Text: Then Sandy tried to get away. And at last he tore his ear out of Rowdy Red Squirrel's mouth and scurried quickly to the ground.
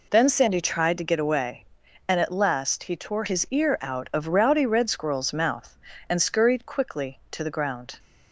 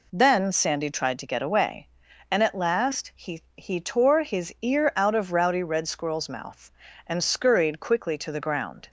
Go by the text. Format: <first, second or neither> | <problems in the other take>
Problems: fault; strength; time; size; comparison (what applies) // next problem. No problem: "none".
first | says "he" twice; at 3.5 s